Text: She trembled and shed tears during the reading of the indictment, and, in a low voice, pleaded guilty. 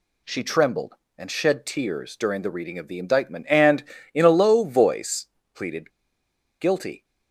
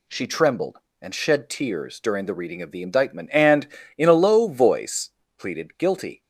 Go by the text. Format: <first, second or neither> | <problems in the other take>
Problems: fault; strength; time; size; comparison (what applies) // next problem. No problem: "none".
second | pauses between "pleaded" and "guilty"; noticeable; at 5.9 s; 0.69 s long